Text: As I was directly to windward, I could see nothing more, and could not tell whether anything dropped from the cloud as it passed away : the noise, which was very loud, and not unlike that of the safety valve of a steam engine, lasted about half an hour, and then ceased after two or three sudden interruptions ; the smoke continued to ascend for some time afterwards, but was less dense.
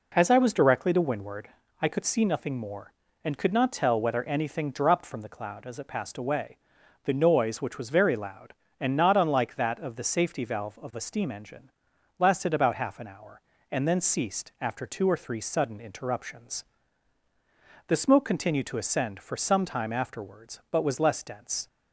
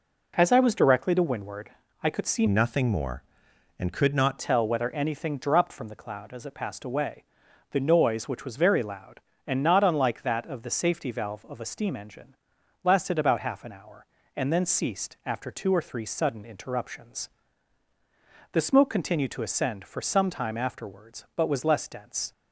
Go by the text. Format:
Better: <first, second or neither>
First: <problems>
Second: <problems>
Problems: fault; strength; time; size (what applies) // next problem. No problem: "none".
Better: first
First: none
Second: changes voice from "nothing" to "not"; from 2.4 to 4.3 s; 1.9 s long